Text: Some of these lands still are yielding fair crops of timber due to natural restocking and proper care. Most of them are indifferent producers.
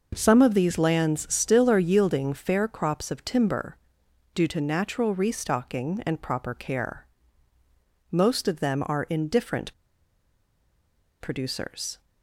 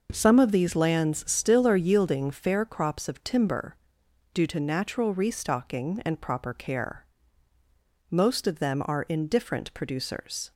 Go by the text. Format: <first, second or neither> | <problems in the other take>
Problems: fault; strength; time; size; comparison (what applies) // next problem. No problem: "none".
second | pauses between "timber" and "due"; noticeable; at 3.7 s; 0.56 s long; noticeable in the second // pauses between "indifferent" and "producers"; strong; at 9.7 s; 1.4 s long